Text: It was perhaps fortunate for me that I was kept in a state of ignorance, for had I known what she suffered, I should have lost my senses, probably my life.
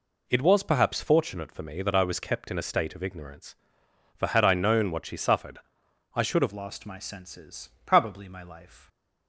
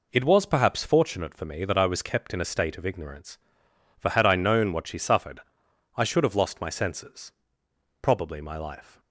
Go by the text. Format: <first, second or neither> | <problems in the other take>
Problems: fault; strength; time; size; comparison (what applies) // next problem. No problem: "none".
second | changes voice at "lost"; from 6.5 s on; 2.3 s long